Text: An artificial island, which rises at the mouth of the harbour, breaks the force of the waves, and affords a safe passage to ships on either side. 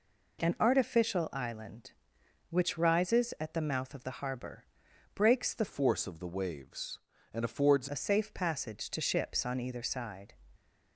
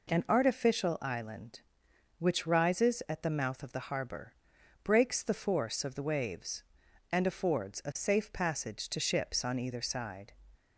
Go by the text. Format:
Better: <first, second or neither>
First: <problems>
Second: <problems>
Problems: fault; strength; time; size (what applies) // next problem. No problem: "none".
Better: second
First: changes voice from "force" to "affords"; from 5.6 to 7.8 s; 2.2 s long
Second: none